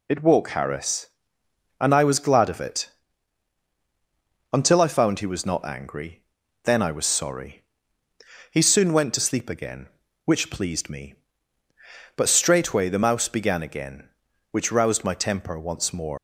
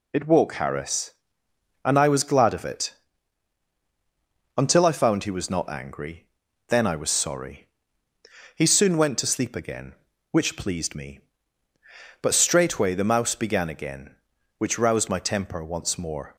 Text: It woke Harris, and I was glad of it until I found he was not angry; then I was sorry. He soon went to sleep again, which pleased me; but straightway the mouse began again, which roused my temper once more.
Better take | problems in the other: second | pauses between "it" and "until"; strong; at 2.8 s; 1.6 s long; strong in the second // leaves "more" unfinished; at 16.1 s; 125 ms

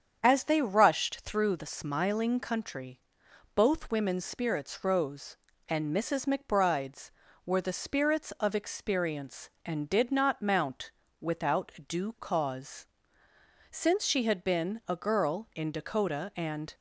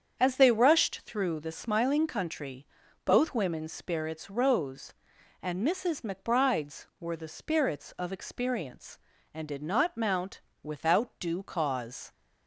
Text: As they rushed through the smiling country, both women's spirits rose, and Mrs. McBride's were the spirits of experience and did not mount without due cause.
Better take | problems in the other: second | starts louder than the rest; strong; until 1.2 s; 7.5 dB; strong in the second // pauses between "mount" and "without"; slight; at 10.8 s; 0.32 s long; slight in the second // pauses between "without" and "due"; slight; at 11.7 s; 0.16 s long // goes on to say "Since she had been a girl in Dakota and"; strong; from 13.6 s on; 3.0 s long

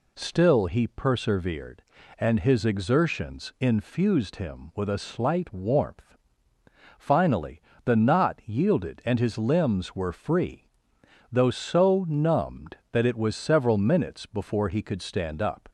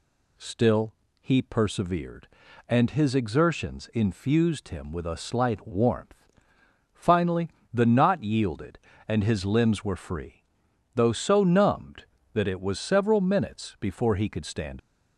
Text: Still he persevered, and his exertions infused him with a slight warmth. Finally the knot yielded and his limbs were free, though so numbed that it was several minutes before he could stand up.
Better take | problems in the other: first | pauses between "Still" and "he"; slight; at 0.9 s; 0.26 s long // pauses between "Finally" and "the"; slight; at 7.4 s; 0.22 s long; slight in the first // stops before "up"; at 14.7 s

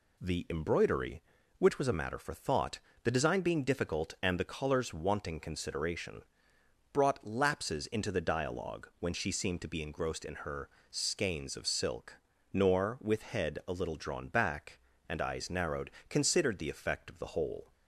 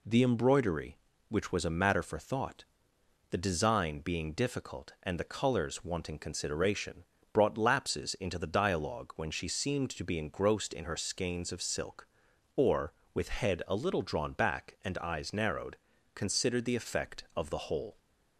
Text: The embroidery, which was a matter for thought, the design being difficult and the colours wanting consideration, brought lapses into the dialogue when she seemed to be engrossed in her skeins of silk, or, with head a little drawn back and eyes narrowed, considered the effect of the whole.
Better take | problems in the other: second | pauses between "her" and "skeins"; slight; at 10.6 s; 0.20 s long // says "nor" for "or"; at 12.5 s

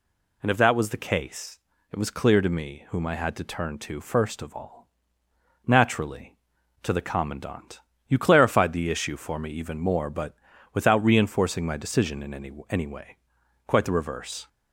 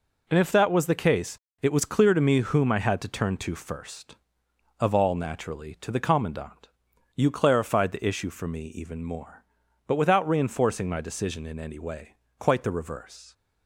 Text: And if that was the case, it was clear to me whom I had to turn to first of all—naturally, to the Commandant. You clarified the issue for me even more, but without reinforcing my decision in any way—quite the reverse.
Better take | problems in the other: second | pauses between "but" and "without"; at 10.3 s; 0.38 s long // says "any" twice; at 12.6 s

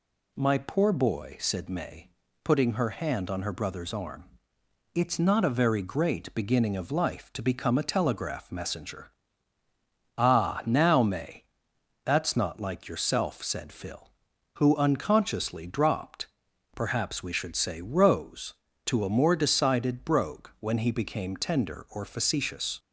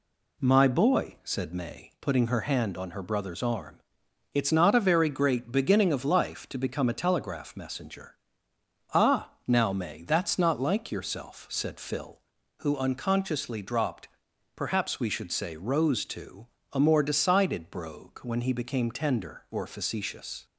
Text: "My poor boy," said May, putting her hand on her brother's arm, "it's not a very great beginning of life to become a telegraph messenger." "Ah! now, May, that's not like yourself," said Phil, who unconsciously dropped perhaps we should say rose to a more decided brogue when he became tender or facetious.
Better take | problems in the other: first | skips "poor"; at 0.6 s // pauses between "dropped" and "perhaps"; noticeable; at 14.0 s; 0.48 s long; noticeable in the first // pauses between "to" and "a"; slight; at 16.4 s; 0.24 s long

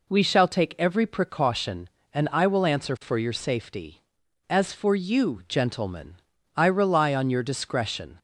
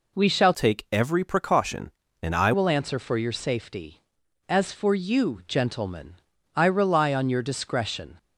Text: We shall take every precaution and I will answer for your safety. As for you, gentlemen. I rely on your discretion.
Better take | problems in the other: first | changes voice from "take" to "I"; from 0.5 to 2.5 s; 2.0 s long

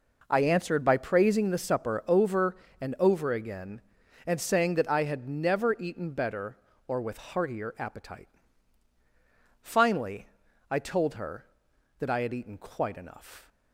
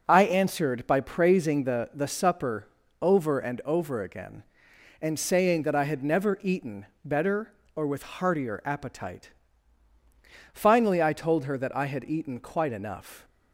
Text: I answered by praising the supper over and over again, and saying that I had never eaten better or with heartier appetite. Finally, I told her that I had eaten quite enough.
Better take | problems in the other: first | says "the" twice; at 1.9 s // pauses between "supper" and "over"; slight; at 2.6 s; 0.34 s long // pauses between "eaten" and "better"; slight; at 6.8 s; 0.20 s long

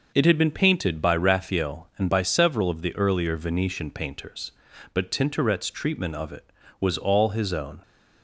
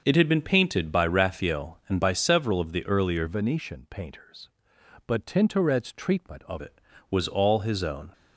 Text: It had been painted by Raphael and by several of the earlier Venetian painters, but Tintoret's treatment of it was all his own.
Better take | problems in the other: first | starts louder than the rest; until 1.0 s; 6.5 dB; noticeable in the first // changes voice from "Venetian" to "of"; from 3.2 to 6.6 s; 3.4 s long

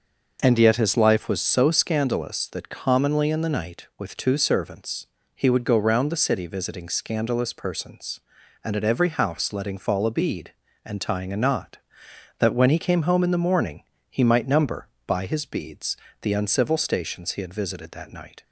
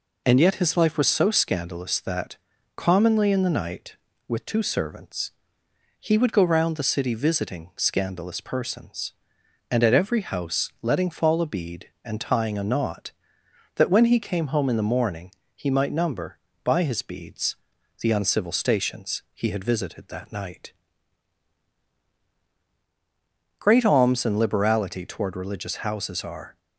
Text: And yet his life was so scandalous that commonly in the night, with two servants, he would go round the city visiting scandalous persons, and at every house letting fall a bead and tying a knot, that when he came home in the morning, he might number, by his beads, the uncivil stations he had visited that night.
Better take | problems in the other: first | pauses between "that" and "commonly"; at 2.3 s; 0.40 s long // goes on to say "Great alms and liberality toward religious houses are"; strong; from 23.5 s on; 2.9 s long

